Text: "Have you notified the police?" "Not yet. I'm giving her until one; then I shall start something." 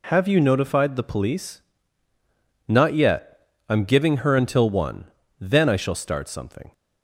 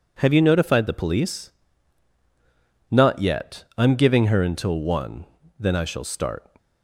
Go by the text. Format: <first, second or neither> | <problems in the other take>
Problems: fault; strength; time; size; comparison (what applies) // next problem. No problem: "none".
first | stops before "something"; at 6.5 s